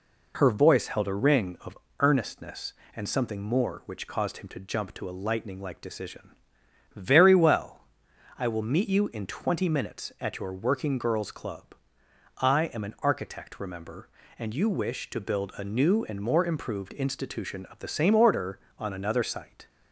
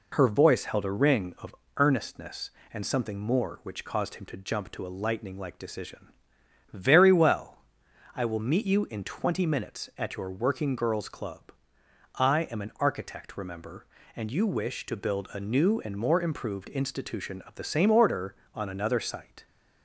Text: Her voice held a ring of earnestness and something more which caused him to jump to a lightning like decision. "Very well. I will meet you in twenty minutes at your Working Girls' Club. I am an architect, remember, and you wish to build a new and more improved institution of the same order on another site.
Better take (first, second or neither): neither